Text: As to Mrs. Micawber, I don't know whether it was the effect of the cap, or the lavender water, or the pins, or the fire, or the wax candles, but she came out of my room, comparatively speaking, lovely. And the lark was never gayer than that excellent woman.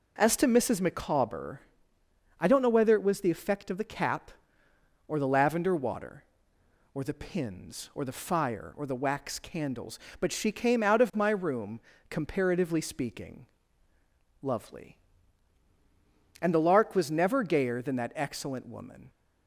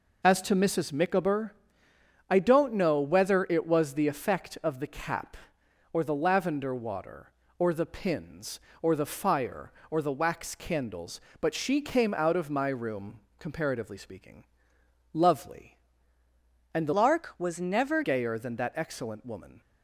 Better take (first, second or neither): first